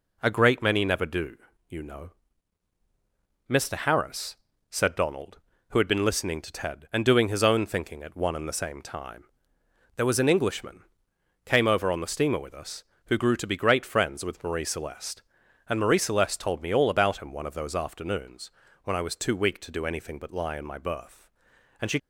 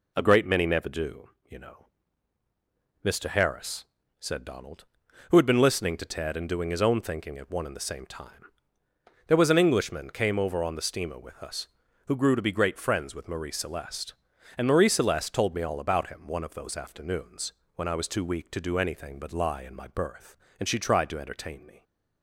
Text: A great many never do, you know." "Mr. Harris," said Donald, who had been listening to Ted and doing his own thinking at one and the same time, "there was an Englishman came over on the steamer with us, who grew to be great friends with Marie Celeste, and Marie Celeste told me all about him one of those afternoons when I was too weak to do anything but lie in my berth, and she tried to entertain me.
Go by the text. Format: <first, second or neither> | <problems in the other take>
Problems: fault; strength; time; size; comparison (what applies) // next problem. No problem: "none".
second | pauses between "Englishman" and "came"; noticeable; at 10.8 s; 0.62 s long // pauses between "afternoons" and "when"; slight; at 18.5 s; 0.34 s long; slight in the second // stops before "tried to entertain me"; at 21.9 s